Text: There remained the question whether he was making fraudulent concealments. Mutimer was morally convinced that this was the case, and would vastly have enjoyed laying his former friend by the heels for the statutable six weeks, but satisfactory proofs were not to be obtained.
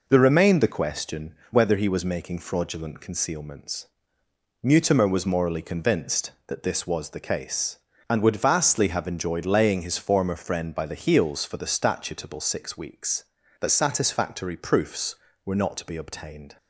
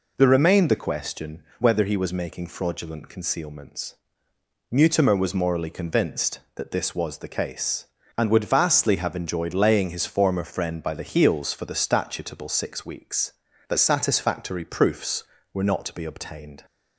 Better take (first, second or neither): second